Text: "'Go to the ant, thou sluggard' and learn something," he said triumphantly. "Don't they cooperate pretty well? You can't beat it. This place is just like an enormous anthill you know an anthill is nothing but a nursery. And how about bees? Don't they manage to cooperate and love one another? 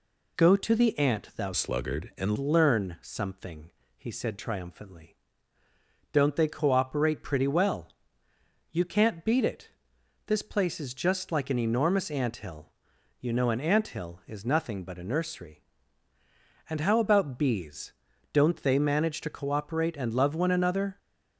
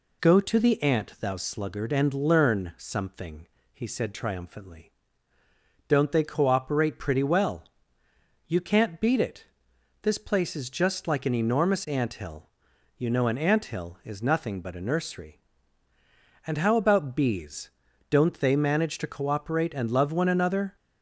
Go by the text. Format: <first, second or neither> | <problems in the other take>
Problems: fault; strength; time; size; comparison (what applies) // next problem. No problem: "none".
second | changes voice from "sluggard" to "and"; from 1.5 to 2.3 s; 0.8 s long // pauses between "anthill" and "you"; noticeable; at 12.6 s; 0.50 s long; noticeable in the second